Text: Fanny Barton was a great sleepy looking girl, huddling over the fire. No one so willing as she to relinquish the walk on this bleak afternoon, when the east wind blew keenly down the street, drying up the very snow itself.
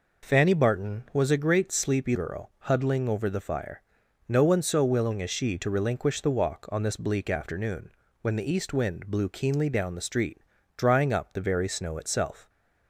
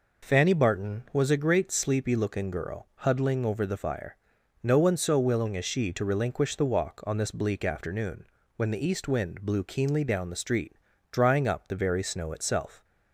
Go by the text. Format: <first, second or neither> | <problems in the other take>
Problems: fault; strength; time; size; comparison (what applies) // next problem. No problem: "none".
second | skips "looking"; at 2.1 s